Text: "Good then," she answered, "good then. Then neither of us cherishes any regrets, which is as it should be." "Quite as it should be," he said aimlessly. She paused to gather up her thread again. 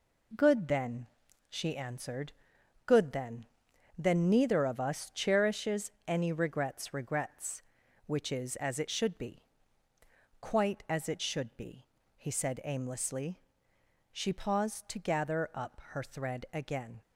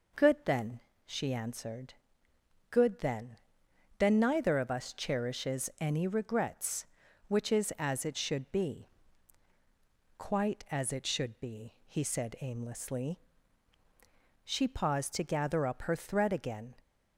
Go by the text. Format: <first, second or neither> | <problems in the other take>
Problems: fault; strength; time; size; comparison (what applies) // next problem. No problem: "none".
second | pauses between "cherishes" and "any"; slight; at 5.9 s; 0.16 s long // says "regrets" twice; at 6.9 s